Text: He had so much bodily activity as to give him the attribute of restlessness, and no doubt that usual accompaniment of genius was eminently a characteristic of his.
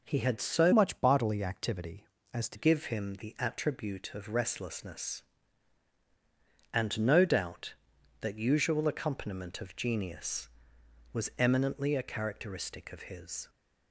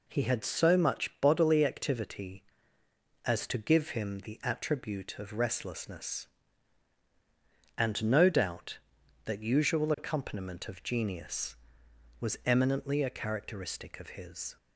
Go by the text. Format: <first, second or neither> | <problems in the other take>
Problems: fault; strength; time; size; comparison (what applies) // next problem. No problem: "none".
second | changes voice from "much" to "to"; from 0.7 to 2.5 s; 1.8 s long